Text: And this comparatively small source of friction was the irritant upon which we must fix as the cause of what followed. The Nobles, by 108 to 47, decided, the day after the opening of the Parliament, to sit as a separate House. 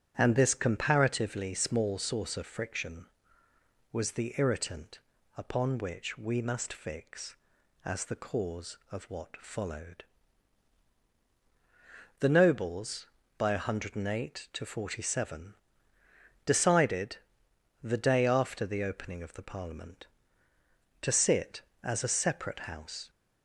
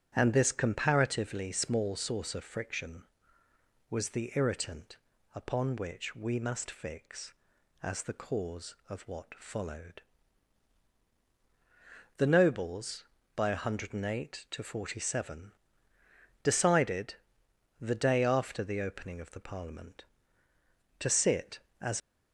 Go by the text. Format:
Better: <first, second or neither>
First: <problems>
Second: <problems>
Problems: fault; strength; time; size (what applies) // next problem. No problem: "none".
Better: first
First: starts louder than the rest; strong; until 1.1 s; 9.5 dB // pauses between "irritant" and "upon"; slight; at 4.9 s; 0.36 s long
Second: starts louder than the rest; strong; until 1.1 s; 9.5 dB // pauses between "irritant" and "upon"; slight; at 4.9 s; 0.36 s long // stops before "a separate House"; at 22.0 s